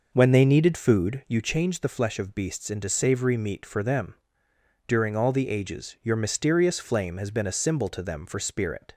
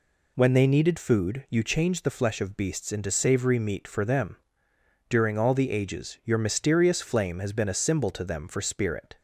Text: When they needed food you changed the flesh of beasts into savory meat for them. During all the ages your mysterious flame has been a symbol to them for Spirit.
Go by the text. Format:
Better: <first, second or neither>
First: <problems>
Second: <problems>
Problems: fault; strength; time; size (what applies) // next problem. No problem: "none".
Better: second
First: starts louder than the rest; noticeable; until 1.3 s; 5.5 dB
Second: none